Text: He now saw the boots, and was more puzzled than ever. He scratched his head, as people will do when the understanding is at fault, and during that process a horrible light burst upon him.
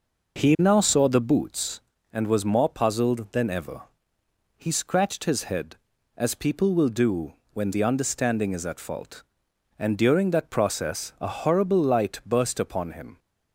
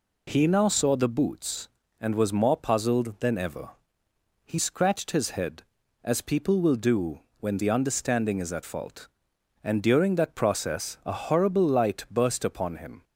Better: second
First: starts louder than the rest; noticeable; until 1.9 s; 5.5 dB // pauses between "do" and "when"; slight; at 7.3 s; 0.20 s long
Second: pauses between "do" and "when"; slight; at 7.1 s; 0.20 s long

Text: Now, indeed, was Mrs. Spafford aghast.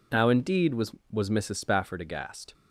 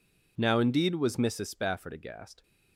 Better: second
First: says "was" twice; at 1.1 s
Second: none

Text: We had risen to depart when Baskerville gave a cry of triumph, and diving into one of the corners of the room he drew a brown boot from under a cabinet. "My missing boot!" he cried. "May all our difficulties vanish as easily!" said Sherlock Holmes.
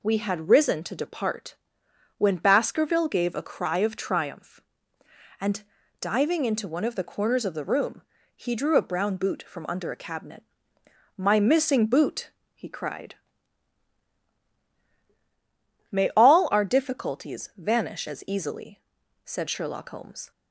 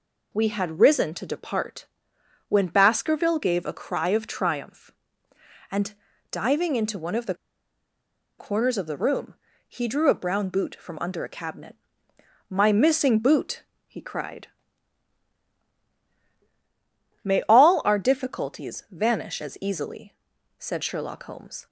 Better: first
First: pauses between "depart" and "when"; noticeable; at 1.5 s; 0.62 s long // pauses between "and" and "diving"; at 5.6 s; 0.38 s long // pauses between "room" and "he"; slight; at 8.0 s; 0.34 s long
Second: pauses between "depart" and "when"; noticeable; at 1.8 s; 0.62 s long // pauses between "and" and "diving"; at 5.9 s; 0.38 s long // pauses between "the" and "corners"; at 7.3 s; 1.0 s long // pauses between "room" and "he"; slight; at 9.3 s; 0.34 s long

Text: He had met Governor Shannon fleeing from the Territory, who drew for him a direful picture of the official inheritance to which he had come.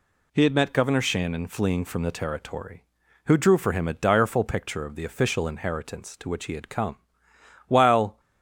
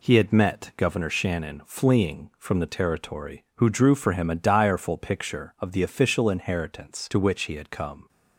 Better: second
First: goes on to say "While"; from 7.6 s on; 0.52 s long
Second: none

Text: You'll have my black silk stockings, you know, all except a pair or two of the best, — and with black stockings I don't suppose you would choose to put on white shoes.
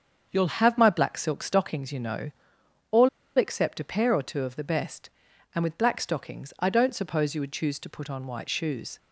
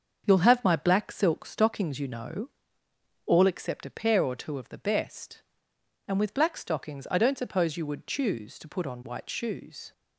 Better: second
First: starts louder than the rest; until 1.3 s; 7 dB // pauses between "all" and "except"; slight; at 3.0 s; 0.29 s long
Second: starts louder than the rest; until 1.2 s; 6.5 dB

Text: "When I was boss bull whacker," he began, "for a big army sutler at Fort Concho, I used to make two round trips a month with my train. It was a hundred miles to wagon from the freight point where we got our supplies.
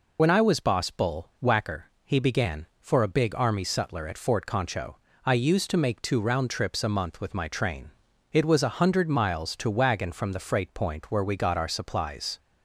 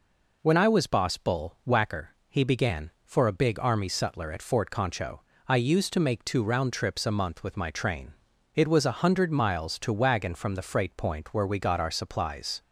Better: second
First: loses the start of "When"; at 0.1 s; 60 ms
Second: none

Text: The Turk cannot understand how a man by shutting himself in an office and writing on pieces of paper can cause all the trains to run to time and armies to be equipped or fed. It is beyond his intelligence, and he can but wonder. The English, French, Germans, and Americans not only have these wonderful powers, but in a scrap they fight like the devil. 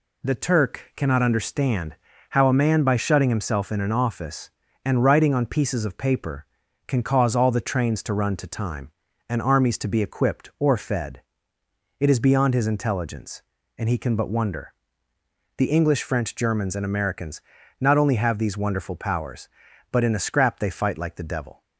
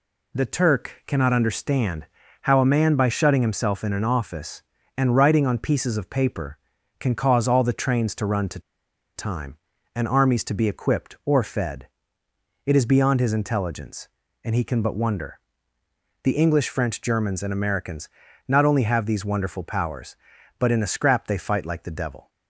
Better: first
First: pauses between "understand" and "how"; slight; at 1.9 s; 0.33 s long // pauses between "Americans" and "not"; at 17.3 s; 0.40 s long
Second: pauses between "understand" and "how"; slight; at 2.0 s; 0.34 s long // pauses between "to" and "time"; noticeable; at 8.5 s; 0.56 s long // pauses between "Americans" and "not"; at 18.0 s; 0.40 s long

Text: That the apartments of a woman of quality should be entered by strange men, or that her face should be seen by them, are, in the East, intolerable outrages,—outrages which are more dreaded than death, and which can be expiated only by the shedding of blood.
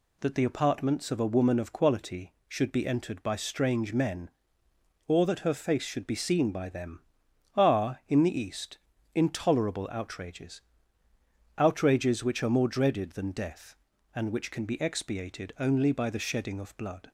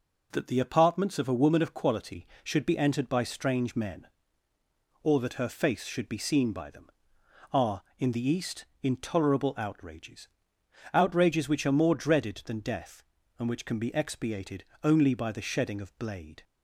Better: first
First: none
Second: pauses between "expiated" and "only"; slight; at 14.6 s; 0.20 s long // says "blade" for "blood"; at 15.9 s

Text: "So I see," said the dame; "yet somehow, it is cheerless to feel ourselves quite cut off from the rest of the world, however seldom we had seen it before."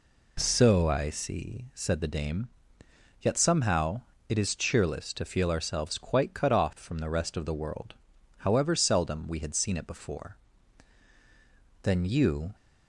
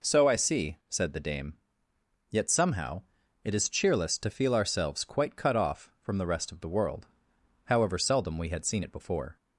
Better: second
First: goes on to say "Then you"; noticeable; from 11.8 s on; 0.72 s long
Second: none

